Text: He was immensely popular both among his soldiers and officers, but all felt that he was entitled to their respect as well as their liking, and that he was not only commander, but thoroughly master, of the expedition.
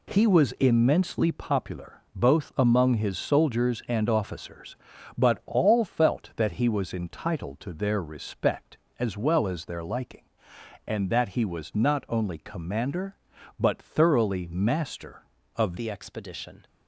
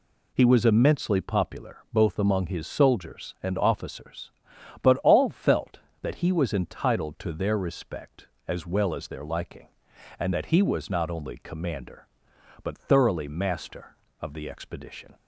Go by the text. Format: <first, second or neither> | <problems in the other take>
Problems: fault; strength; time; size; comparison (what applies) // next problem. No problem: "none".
second | changes voice at "the"; from 15.7 s on; 0.9 s long